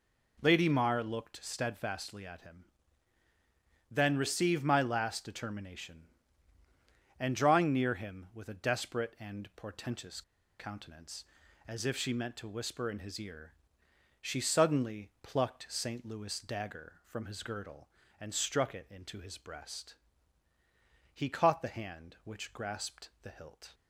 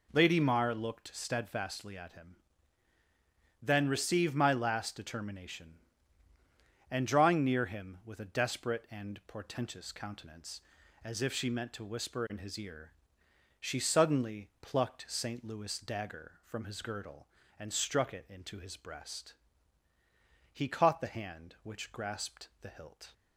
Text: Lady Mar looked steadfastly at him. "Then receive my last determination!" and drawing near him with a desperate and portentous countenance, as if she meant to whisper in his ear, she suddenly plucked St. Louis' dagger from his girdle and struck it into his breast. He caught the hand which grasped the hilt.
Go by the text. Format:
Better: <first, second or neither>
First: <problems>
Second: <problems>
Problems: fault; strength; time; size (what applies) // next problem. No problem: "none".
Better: second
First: pauses between "portentous" and "countenance"; at 10.2 s; 0.37 s long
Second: none